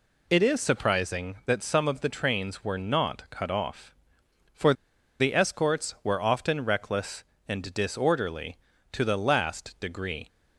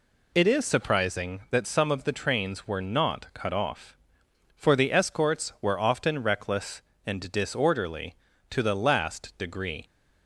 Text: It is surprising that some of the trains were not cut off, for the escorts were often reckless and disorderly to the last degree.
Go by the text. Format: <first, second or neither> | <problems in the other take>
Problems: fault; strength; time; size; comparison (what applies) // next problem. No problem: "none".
second | pauses between "for" and "the"; noticeable; at 4.7 s; 0.46 s long